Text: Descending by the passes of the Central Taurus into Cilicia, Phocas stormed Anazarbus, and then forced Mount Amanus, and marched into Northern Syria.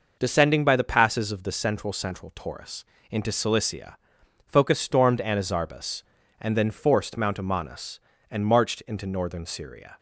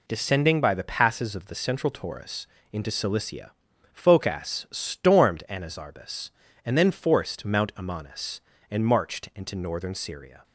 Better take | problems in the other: second | says "Central" twice; at 1.9 s // pauses between "Taurus" and "into"; slight; at 2.8 s; 0.26 s long; slight in the second

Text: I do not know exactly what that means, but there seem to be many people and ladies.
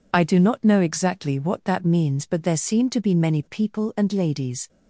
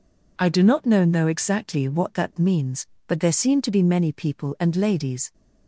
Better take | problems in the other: first | says "know" twice; at 1.0 s

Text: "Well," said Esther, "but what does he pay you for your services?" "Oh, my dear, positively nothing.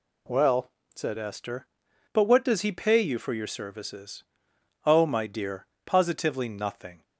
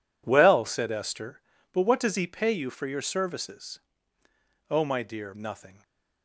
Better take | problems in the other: first | skips "positively"; at 5.3 s

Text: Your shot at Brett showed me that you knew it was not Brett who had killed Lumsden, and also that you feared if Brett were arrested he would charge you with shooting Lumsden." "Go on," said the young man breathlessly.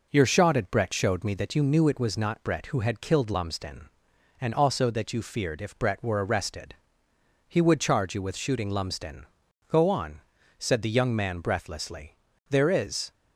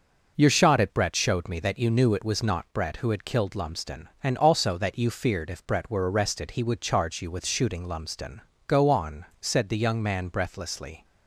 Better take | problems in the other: second | pauses between "arrested" and "he"; noticeable; at 6.7 s; 0.76 s long // goes on to say "There is"; from 12.5 s on; 0.60 s long

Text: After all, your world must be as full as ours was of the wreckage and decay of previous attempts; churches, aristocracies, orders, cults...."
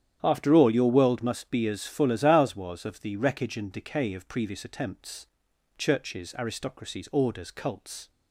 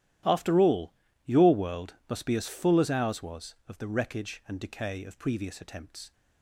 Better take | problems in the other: first | starts louder than the rest; strong; until 1.5 s; 12.5 dB; strong in the first // stops before "churches aristocracies orders cults"; at 6.1 s

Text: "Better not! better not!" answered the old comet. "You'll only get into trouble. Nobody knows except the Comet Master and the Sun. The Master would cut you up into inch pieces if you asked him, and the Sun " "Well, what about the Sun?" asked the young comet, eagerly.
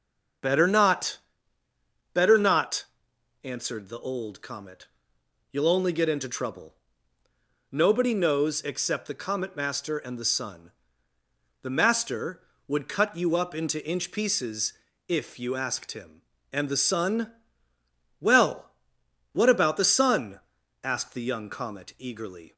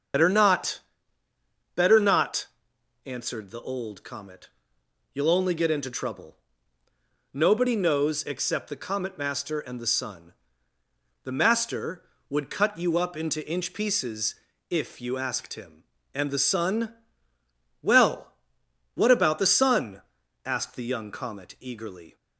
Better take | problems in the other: first | loses the start of "Better"; at 0.1 s; 110 ms // starts louder than the rest; until 2.1 s; 7 dB; also in the first // pauses between "pieces" and "if"; slight; at 14.3 s; 0.36 s long; slight in the first

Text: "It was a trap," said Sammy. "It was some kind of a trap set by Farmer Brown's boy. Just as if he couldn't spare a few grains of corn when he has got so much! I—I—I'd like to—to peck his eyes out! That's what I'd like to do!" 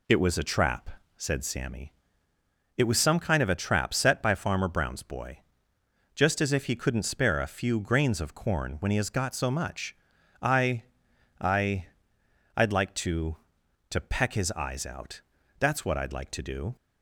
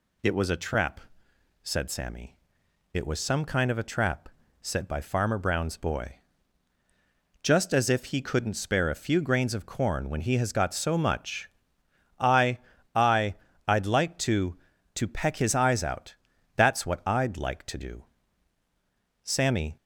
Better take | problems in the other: first | pauses between "trap" and "set"; slight; at 4.2 s; 0.32 s long // goes on to say "Sammy"; from 19.2 s on; 0.54 s long

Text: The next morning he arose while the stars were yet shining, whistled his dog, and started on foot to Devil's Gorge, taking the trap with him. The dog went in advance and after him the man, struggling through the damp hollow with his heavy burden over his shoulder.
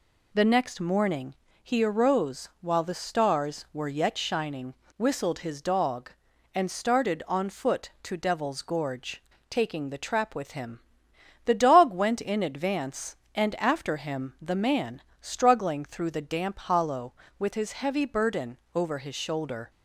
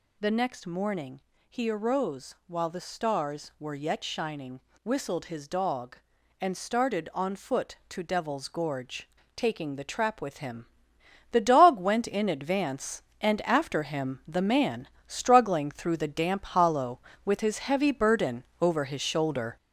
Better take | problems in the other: first | gets louder; noticeable; throughout; 5.5 dB // pauses between "morning" and "he"; slight; at 1.2 s; 0.28 s long; slight in the first // pauses between "burden" and "over"; slight; at 18.4 s; 0.18 s long; slight in the first

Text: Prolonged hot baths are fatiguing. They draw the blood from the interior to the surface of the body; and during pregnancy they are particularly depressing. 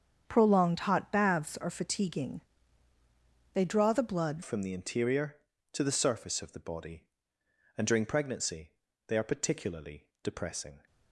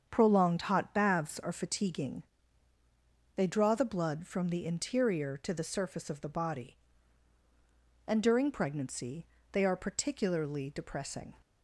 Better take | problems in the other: second | starts louder than the rest; strong; until 1.2 s; 7.5 dB; also in the second // changes voice at "from"; from 4.4 s on; 6.4 s long // pauses between "pregnancy" and "they"; slight; at 8.7 s; 0.34 s long; slight in the second

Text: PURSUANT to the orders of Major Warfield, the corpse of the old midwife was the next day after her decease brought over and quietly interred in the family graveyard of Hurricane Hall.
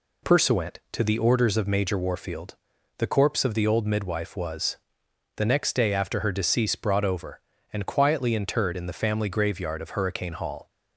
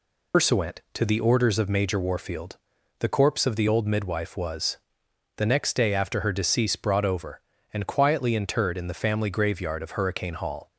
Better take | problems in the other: first | loses the start of "PURSUANT"; at 0.3 s; 90 ms // pauses between "was" and "the"; noticeable; at 4.7 s; 0.58 s long; noticeable in the first

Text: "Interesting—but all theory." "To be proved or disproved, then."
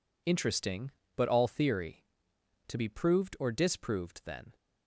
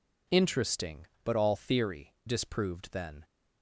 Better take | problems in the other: first | skips "To be proved or"; at 2.1 s

